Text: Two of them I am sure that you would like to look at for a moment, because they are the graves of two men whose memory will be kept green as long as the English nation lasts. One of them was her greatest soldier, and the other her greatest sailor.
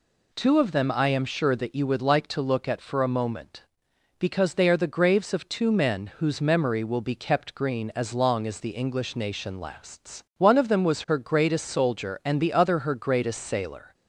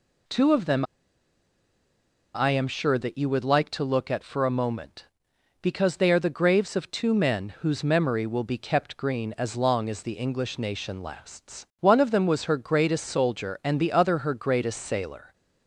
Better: first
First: none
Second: pauses between "them" and "I"; strong; at 0.8 s; 1.5 s long

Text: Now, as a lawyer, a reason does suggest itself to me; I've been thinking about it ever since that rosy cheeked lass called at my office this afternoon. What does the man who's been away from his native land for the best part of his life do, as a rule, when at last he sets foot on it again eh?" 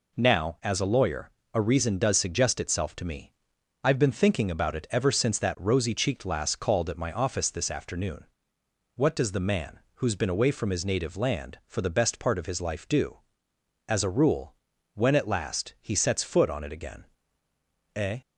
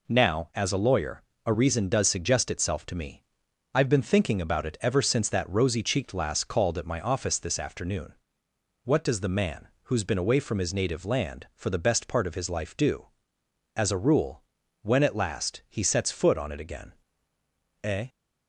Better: neither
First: pauses between "again" and "eh"; noticeable; at 17.0 s; 0.90 s long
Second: pauses between "again" and "eh"; noticeable; at 16.9 s; 0.90 s long

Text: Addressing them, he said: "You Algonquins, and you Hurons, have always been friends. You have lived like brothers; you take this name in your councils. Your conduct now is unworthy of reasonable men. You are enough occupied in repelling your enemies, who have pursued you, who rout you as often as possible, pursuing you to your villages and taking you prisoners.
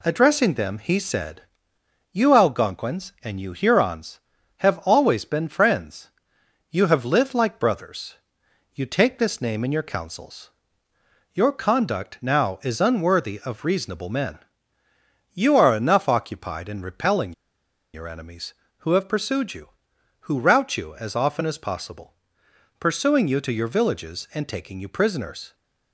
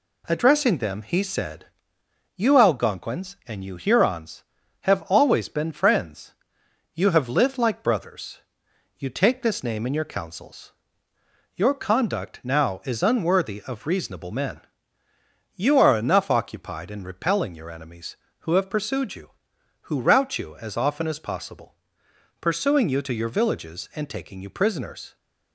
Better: second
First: pauses between "repelling" and "your"; noticeable; at 17.3 s; 0.62 s long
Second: none

